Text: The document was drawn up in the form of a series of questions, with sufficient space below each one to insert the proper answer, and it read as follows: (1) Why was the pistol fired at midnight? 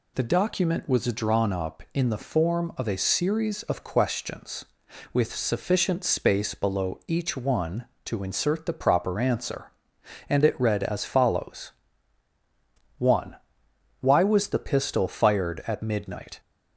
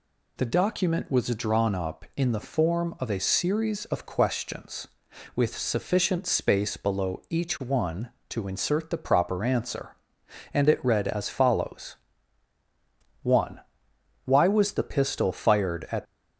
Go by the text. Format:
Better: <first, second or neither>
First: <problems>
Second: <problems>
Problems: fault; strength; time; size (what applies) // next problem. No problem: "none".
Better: first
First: none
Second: stops before "midnight"; at 16.0 s